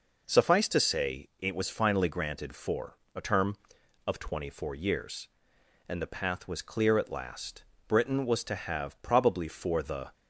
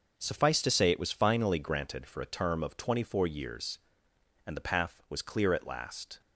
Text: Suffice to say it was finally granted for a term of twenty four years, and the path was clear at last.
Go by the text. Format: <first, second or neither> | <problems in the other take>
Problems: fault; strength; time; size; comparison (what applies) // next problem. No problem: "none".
second | pauses between "for" and "a"; slight; at 2.9 s; 0.18 s long // goes on to say "Britain was to have probably for the"; strong; from 7.8 s on; 2.2 s long